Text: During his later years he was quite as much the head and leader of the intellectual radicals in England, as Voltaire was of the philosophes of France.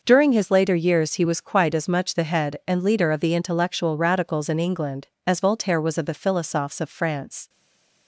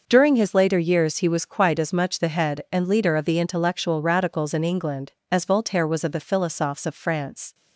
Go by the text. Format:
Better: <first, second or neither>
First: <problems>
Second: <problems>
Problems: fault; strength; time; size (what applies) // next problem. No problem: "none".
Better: second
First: stays silent after the last word; slight; from 7.4 s on; 0.6 s long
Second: none